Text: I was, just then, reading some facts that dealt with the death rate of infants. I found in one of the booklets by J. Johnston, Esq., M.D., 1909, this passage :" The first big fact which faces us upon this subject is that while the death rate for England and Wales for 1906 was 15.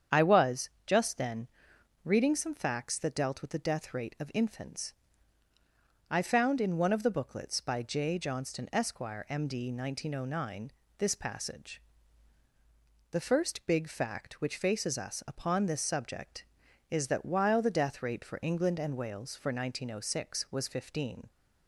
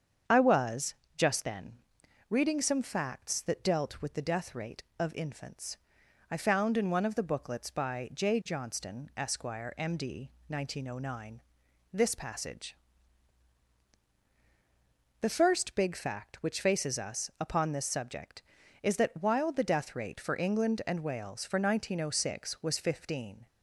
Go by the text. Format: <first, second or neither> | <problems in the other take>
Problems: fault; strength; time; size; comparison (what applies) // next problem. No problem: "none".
neither | starts louder than the rest; strong; the same in both